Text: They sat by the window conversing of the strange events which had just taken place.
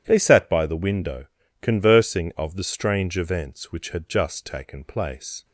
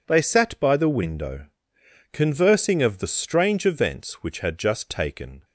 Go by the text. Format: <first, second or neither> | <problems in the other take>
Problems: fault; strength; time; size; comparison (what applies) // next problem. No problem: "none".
first | pauses between "window" and "conversing"; noticeable; at 1.4 s; 0.66 s long; slight in the first // stops before "place"; at 5.4 s